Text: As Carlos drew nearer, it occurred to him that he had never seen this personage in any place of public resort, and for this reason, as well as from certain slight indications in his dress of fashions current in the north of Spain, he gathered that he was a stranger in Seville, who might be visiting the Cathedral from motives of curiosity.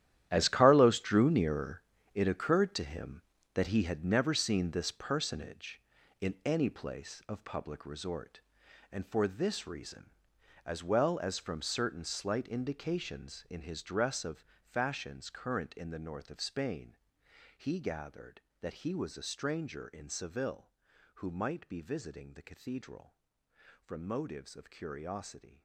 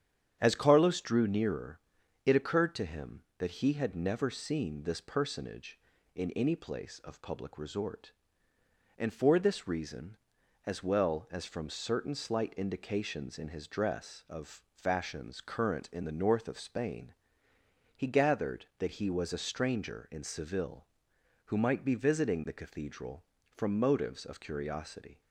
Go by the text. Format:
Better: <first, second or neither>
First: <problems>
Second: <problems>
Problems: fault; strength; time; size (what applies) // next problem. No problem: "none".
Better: second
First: gets quieter; strong; throughout; 13.5 dB // starts louder than the rest; strong; until 1.3 s; 11.5 dB // pauses between "of" and "fashions"; slight; at 14.4 s; 0.21 s long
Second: starts louder than the rest; strong; until 1.4 s; 9 dB